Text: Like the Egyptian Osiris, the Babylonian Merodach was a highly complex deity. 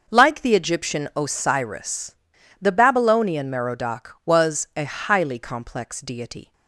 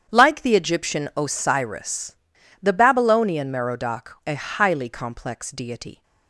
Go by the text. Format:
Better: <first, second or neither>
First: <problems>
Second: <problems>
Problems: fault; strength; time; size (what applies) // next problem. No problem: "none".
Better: first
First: starts louder than the rest; noticeable; until 1.0 s; 6 dB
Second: starts louder than the rest; strong; until 1.1 s; 8.5 dB // skips "was"; at 4.2 s